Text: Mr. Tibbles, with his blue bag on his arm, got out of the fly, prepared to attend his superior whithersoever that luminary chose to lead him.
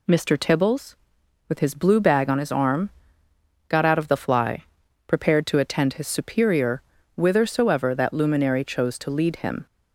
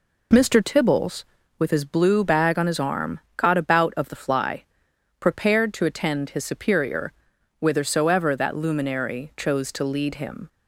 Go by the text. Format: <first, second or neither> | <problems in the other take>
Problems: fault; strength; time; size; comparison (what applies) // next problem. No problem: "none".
first | says "about" for "out"; at 3.5 s // pauses between "superior" and "whithersoever"; noticeable; at 7.1 s; 0.48 s long; slight in the first